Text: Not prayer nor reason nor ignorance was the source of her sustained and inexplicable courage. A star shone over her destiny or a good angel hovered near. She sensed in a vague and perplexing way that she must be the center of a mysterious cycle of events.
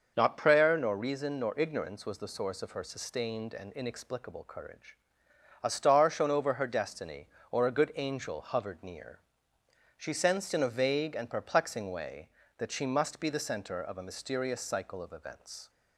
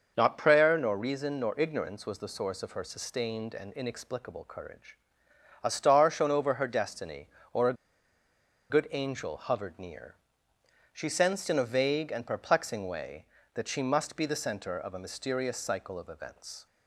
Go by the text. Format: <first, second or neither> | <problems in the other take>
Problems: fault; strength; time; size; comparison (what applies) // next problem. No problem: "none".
first | starts louder than the rest; noticeable; until 1.1 s; 6 dB; noticeable in the first // pauses between "a" and "good"; noticeable; at 7.7 s; 0.95 s long